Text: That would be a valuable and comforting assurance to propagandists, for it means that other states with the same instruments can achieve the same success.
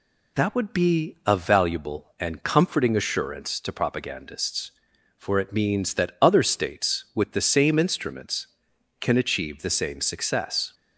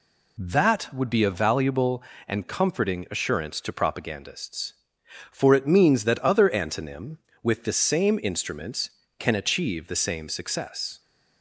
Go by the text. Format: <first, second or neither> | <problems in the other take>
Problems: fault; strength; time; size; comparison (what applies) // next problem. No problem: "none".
first | says "antonym" for "states"; at 6.5 s